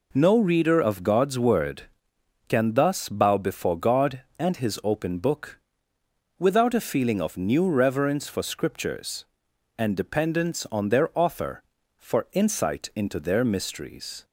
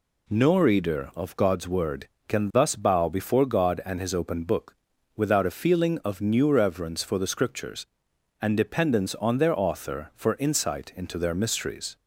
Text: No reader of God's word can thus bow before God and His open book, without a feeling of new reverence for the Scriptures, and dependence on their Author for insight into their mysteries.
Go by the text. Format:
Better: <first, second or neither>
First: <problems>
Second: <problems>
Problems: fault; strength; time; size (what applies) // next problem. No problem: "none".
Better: second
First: skips "the"; at 8.4 s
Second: none